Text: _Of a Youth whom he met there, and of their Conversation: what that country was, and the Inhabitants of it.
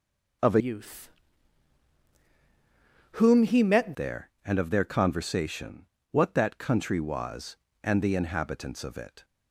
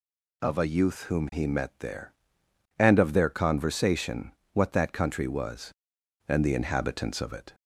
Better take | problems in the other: second | changes voice from "Youth" to "met"; from 0.5 to 3.9 s; 3.4 s long // pauses between "Youth" and "whom"; strong; at 1.0 s; 2.0 s long

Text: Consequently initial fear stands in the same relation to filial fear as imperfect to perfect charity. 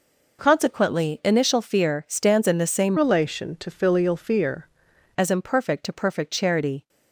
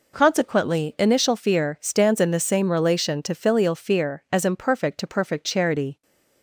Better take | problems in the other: second | changes voice from "relation" to "fear"; from 2.9 to 4.6 s; 1.7 s long

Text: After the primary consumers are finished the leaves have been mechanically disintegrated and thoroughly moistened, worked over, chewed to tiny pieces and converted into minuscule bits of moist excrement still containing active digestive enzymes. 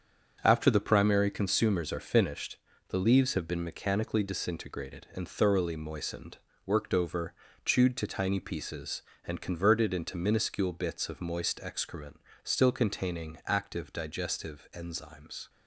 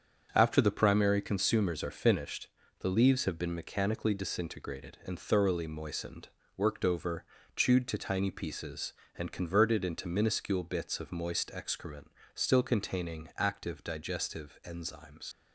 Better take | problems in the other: first | starts louder than the rest; strong; until 1.3 s; 7 dB; strong in the first // pauses between "finished" and "the"; slight; at 2.4 s; 0.32 s long; slight in the first // pauses between "excrement" and "still"; slight; at 12.1 s; 0.24 s long; slight in the first // leaves "enzymes" unfinished; at 15.3 s; 85 ms

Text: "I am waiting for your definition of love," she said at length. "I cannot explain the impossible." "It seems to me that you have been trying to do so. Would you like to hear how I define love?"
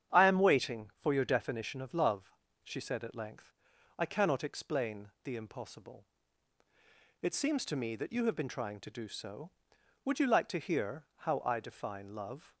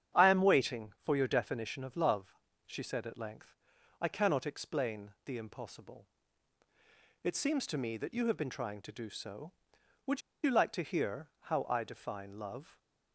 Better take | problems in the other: first | starts louder than the rest; strong; until 1.2 s; 9 dB; strong in the first // pauses between "Would" and "you"; slight; at 10.2 s; 0.23 s long

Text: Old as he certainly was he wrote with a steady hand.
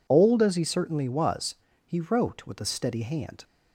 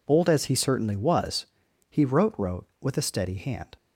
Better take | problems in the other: first | pauses between "was" and "he"; at 1.4 s; 0.44 s long; slight in the first // says "wrote" twice; at 2.3 s

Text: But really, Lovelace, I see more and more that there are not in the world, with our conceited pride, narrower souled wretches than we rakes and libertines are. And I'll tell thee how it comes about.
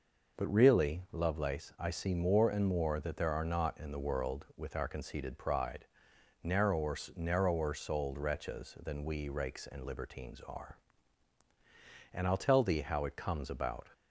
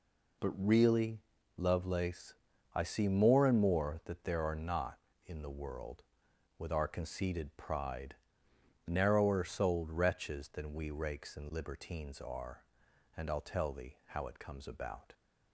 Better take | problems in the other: second | says "narrower" twice; at 7.1 s

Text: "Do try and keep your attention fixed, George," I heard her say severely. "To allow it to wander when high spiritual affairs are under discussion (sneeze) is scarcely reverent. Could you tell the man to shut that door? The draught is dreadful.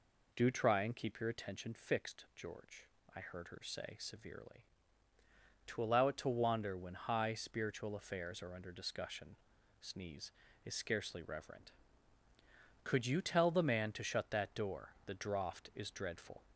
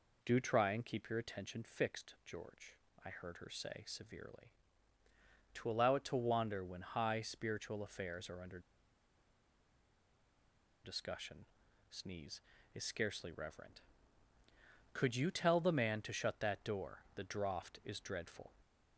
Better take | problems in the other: first | pauses between "under" and "discussion"; strong; at 8.5 s; 2.2 s long

